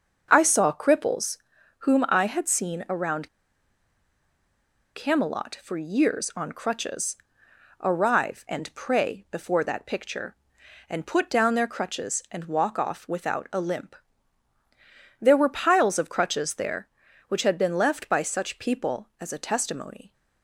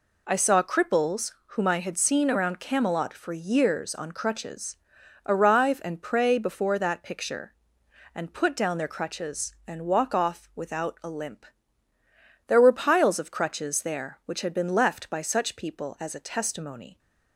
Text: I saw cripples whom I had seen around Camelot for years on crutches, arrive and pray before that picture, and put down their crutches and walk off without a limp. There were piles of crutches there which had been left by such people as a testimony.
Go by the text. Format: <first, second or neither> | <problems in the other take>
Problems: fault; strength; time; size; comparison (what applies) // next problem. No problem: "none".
second | starts louder than the rest; until 1.3 s; 6 dB // pauses between "cripples" and "whom"; at 1.3 s; 0.42 s long // pauses between "around" and "Camelot"; strong; at 3.2 s; 1.6 s long